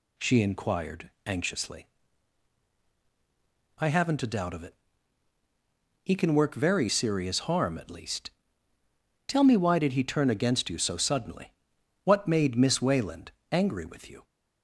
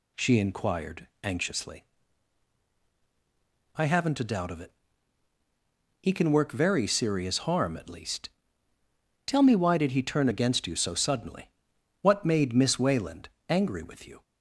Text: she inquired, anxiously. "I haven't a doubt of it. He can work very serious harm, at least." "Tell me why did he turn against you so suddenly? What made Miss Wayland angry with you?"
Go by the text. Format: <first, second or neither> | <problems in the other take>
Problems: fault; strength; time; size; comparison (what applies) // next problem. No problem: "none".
neither | pauses between "Wayland" and "angry"; slight; the same in both